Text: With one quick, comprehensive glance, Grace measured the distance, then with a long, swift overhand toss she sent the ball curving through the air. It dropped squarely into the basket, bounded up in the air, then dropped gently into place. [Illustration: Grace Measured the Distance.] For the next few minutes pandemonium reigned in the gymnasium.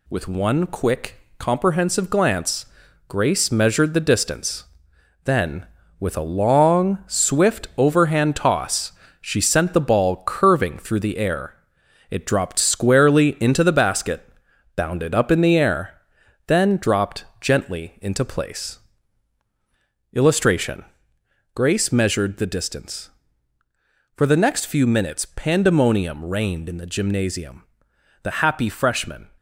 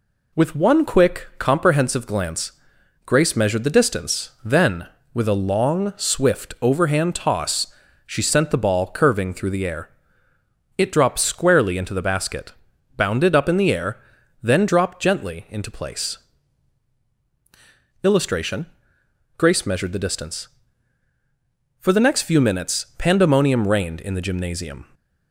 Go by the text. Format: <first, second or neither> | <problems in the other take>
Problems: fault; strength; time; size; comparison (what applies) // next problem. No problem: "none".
second | pauses between "toss" and "she"; slight; at 8.9 s; 0.30 s long; also in the second // goes on to say "The happy freshmen"; noticeable; from 28.2 s on; 1.0 s long